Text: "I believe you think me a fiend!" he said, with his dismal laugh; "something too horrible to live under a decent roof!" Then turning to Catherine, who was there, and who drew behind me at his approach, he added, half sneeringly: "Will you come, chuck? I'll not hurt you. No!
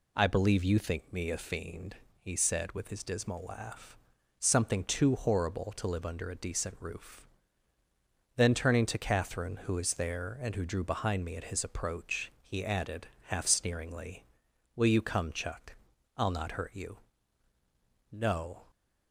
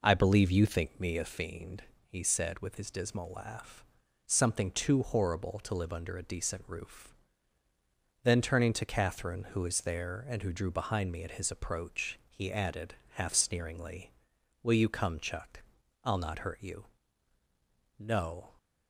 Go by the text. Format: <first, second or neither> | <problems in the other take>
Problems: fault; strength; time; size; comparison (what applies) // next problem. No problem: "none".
first | starts louder than the rest; noticeable; until 1.3 s; 4.5 dB